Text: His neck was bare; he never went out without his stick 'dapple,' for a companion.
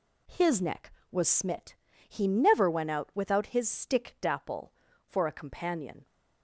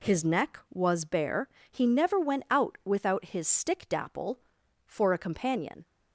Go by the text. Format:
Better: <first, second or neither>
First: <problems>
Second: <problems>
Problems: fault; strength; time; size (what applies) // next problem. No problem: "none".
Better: second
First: says "smit" for "bare"; at 1.2 s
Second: none